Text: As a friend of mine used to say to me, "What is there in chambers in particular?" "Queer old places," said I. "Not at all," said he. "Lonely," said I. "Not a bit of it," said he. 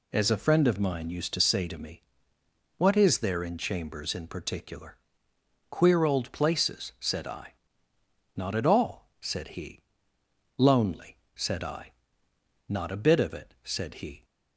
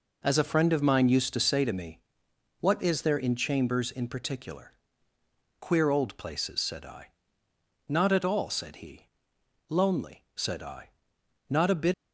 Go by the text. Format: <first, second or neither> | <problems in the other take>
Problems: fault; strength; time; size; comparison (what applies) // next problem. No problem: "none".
first | stops before "of it said he"; at 11.9 s